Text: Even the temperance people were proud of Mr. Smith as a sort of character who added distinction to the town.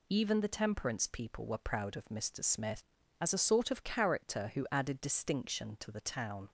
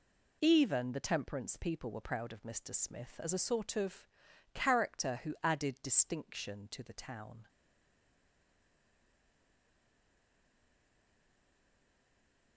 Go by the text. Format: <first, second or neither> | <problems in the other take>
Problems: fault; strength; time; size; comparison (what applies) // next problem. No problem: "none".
first | pauses between "of" and "character"; noticeable; at 4.0 s; 0.46 s long // stays silent after the last word; strong; from 7.4 s on; 5.1 s long